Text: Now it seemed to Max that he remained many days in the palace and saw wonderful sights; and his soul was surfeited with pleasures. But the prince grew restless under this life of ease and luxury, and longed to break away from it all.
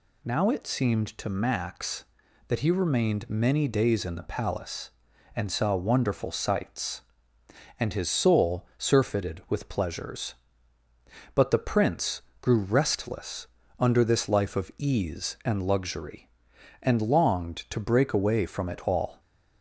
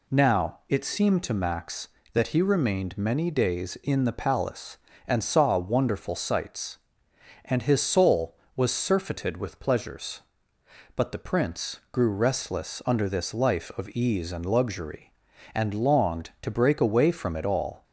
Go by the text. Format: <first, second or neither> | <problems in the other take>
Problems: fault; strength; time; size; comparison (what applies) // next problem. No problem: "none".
second | skips "was"; at 8.7 s // pauses between "prince" and "grew"; slight; at 12.2 s; 0.20 s long // pauses between "restless" and "under"; slight; at 13.4 s; 0.32 s long